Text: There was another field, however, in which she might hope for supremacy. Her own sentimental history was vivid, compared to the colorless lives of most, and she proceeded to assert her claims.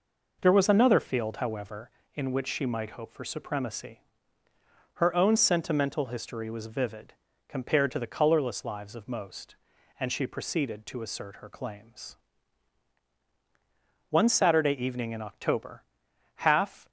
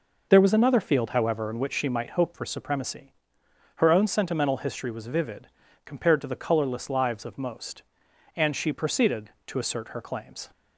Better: second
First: goes on to say "One Saturday evening in October half"; strong; from 14.1 s on; 2.7 s long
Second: none

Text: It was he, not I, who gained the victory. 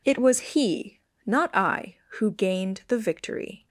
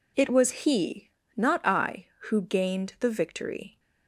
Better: neither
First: none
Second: none

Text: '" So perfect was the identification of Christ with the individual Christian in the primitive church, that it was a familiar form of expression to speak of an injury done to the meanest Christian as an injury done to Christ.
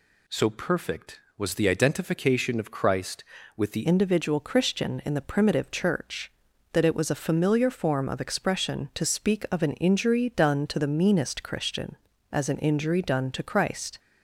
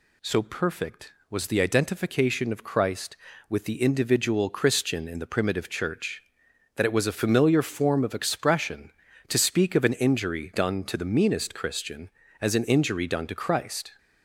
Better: second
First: changes voice at "individual"; from 3.8 s on; 10.1 s long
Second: none

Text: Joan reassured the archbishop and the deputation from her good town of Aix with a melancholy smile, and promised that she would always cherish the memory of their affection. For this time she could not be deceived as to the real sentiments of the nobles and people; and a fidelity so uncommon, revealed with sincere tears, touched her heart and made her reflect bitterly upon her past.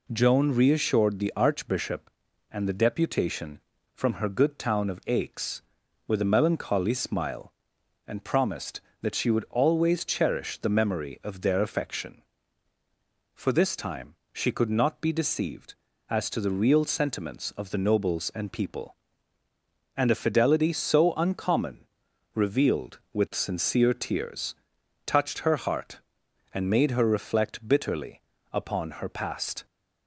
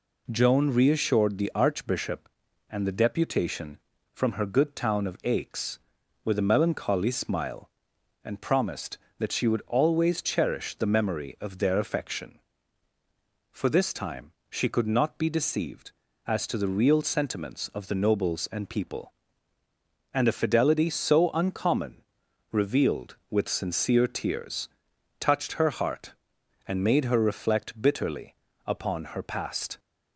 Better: neither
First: pauses between "time" and "she"; slight; at 14.1 s; 0.18 s long // pauses between "bitterly" and "upon"; slight; at 28.2 s; 0.32 s long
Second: pauses between "time" and "she"; slight; at 14.3 s; 0.18 s long // pauses between "bitterly" and "upon"; slight; at 28.3 s; 0.32 s long

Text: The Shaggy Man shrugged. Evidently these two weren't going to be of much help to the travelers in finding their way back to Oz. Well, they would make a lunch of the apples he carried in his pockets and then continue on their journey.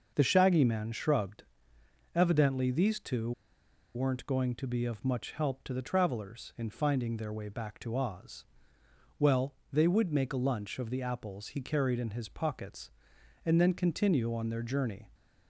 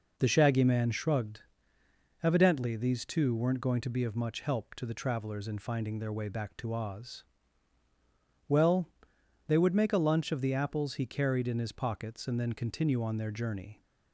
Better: second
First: starts louder than the rest; noticeable; until 1.1 s; 6 dB // pauses between "two" and "weren't"; noticeable; at 3.3 s; 0.63 s long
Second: none

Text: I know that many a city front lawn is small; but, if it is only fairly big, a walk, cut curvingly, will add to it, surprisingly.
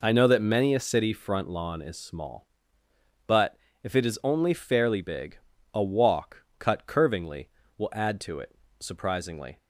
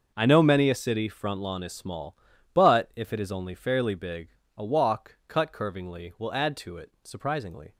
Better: first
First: none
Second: starts louder than the rest; noticeable; until 1.1 s; 6 dB // skips "that"; at 0.4 s

